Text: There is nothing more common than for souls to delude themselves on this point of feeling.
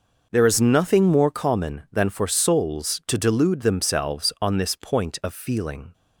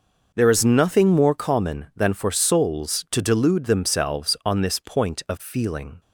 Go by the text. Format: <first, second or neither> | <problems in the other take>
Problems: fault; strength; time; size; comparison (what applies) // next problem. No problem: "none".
neither | none